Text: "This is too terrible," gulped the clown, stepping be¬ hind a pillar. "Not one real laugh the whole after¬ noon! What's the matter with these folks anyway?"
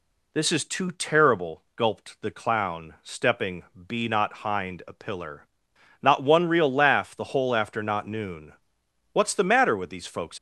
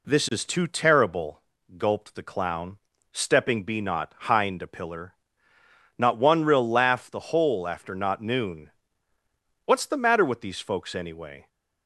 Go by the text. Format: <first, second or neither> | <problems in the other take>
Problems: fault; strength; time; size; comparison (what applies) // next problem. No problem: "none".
second | pauses between "stepping" and "be"; slight; at 3.6 s; 0.26 s long // stops before "anyway"; at 10.3 s